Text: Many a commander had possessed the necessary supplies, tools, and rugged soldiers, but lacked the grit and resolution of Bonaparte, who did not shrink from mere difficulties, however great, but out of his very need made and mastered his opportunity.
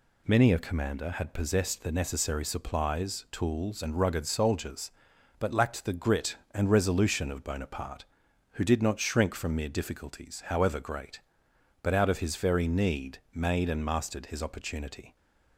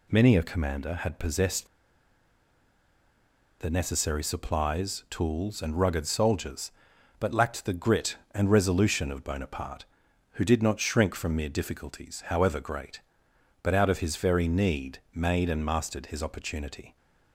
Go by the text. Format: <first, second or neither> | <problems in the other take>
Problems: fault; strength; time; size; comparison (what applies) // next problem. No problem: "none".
first | pauses between "possessed" and "the"; strong; at 1.6 s; 1.9 s long // pauses between "need" and "made"; slight; at 14.9 s; 0.16 s long; slight in the first